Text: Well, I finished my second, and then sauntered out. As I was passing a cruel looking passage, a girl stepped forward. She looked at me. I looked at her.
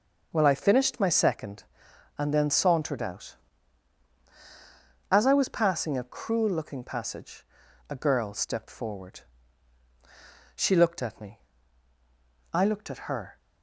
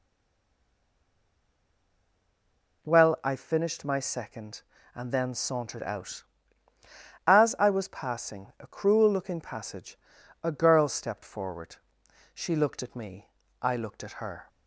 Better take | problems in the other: first | stays silent before the first word; strong; until 2.8 s; 2.8 s long

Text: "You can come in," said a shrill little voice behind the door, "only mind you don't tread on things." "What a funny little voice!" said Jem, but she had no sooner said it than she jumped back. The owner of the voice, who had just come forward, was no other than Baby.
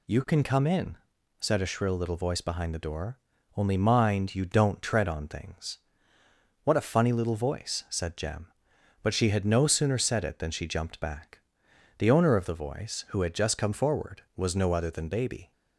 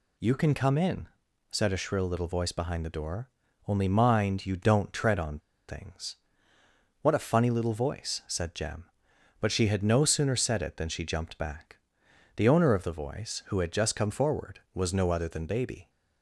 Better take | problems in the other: first | pauses between "on" and "things"; slight; at 5.3 s; 0.29 s long

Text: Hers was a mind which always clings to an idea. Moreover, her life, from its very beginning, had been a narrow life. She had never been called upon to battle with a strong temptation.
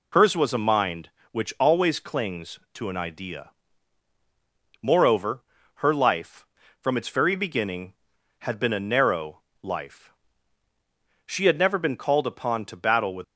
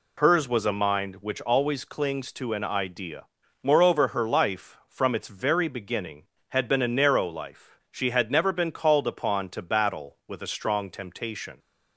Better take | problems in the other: second | pauses between "narrow" and "life"; slight; at 9.3 s; 0.24 s long // stops before "a strong temptation"; at 13.2 s

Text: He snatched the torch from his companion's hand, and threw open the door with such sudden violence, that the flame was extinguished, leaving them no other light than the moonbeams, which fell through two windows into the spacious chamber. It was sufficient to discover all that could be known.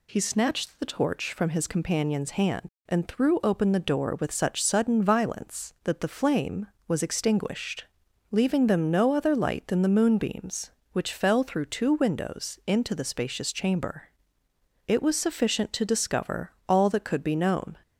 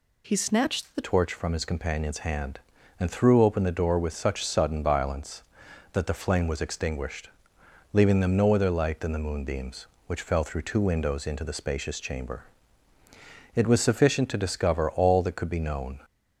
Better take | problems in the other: first | changes voice at "torch"; from 1.0 s on; 15.0 s long

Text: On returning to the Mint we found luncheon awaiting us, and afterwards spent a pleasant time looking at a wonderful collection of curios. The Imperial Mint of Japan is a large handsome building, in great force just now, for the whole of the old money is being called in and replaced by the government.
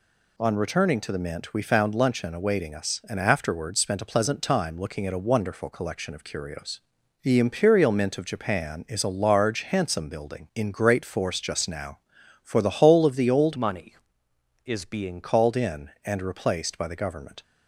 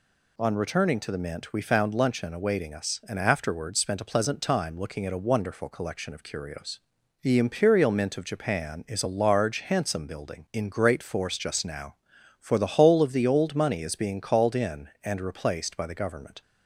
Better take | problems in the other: second | changes voice from "money" to "being"; from 13.5 to 15.2 s; 1.7 s long

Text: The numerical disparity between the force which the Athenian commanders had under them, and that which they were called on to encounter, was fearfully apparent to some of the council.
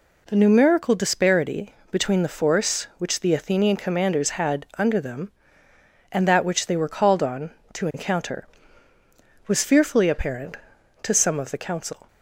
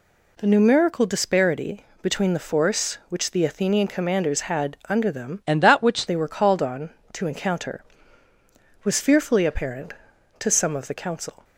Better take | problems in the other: first | pauses between "disparity" and "between"; slight; at 1.8 s; 0.16 s long; slight in the first // changes voice from "and" to "which"; from 5.4 to 6.0 s; 0.6 s long

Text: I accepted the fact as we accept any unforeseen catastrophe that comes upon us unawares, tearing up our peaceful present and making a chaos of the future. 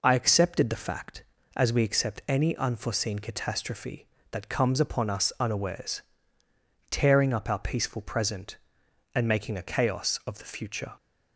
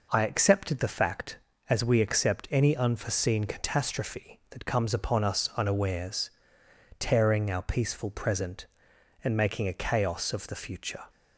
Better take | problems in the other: first | skips "up"; at 7.5 s

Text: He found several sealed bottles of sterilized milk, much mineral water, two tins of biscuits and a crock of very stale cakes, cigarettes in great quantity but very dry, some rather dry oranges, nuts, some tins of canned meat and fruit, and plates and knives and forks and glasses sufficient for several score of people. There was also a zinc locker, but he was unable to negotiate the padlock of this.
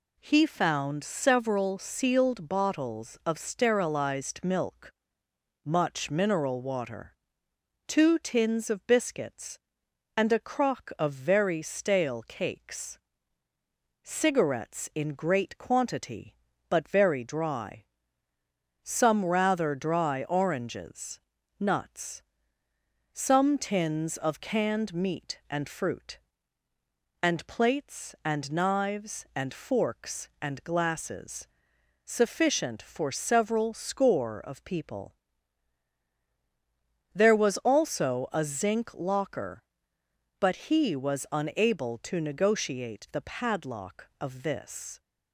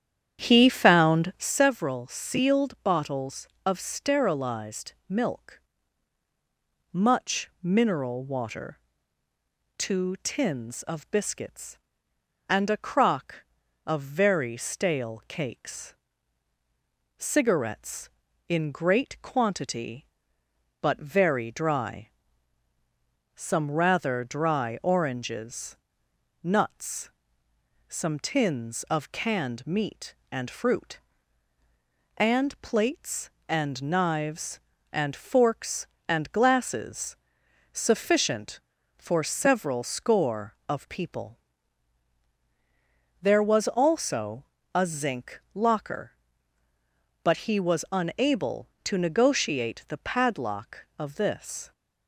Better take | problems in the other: first | starts louder than the rest; strong; until 1.6 s; 9.5 dB // pauses between "glasses" and "sufficient"; noticeable; at 37.1 s; 0.56 s long; noticeable in the first // pauses between "also" and "a"; slight; at 44.4 s; 0.28 s long

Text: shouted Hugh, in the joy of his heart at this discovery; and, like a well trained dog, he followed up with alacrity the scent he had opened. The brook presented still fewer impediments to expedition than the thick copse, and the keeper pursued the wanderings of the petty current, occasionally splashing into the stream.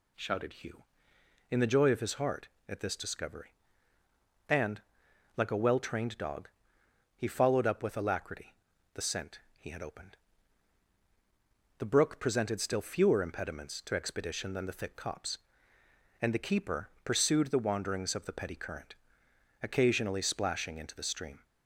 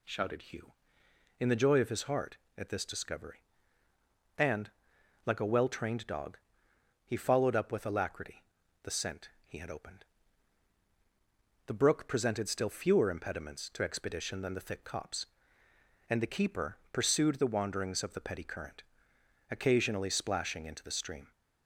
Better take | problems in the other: neither | pauses between "alacrity" and "the"; the same in both // pauses between "scent" and "he"; slight; the same in both

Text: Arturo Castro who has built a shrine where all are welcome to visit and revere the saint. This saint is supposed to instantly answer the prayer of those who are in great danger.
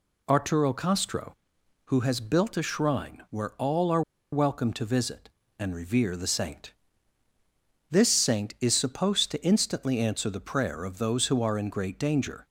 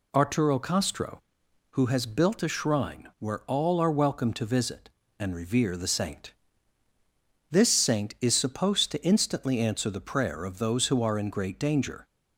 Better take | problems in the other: second | pauses between "are" and "welcome"; slight; at 4.0 s; 0.31 s long

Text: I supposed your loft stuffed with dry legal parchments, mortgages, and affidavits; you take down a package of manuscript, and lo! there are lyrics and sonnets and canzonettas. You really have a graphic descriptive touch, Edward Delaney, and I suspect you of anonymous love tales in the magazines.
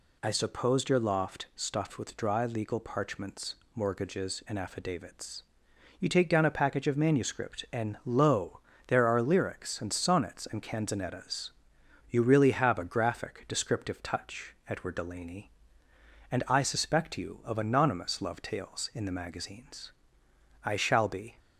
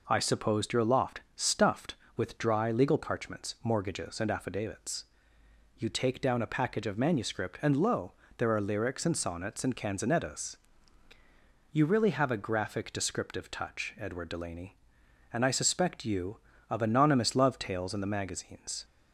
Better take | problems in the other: second | goes on to say "I shall be"; noticeable; from 20.6 s on; 0.74 s long

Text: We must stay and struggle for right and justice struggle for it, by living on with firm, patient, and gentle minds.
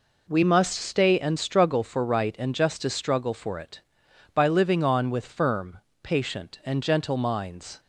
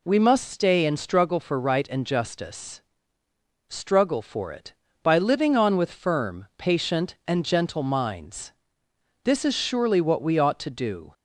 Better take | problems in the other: first | pauses between "justice" and "struggle"; noticeable; at 2.8 s; 0.90 s long // goes on to say "This is surely what we ought to do"; strong; from 9.2 s on; 1.8 s long

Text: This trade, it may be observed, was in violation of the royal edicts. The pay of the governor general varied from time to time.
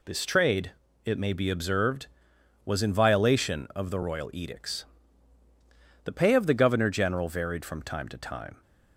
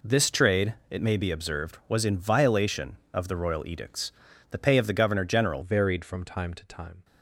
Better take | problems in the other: first | changes voice at "varied"; from 5.6 s on; 1.4 s long

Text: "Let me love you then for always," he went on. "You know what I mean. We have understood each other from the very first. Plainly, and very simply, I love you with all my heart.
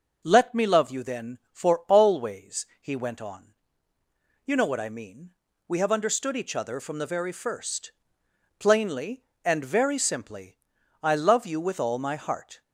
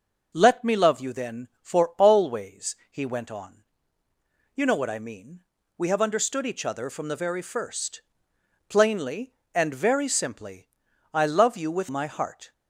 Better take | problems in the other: first | skips "all"; at 11.8 s

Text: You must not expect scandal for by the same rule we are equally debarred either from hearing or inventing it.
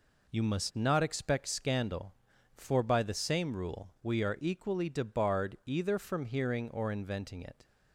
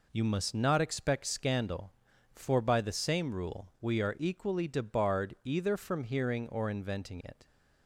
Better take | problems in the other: neither | none

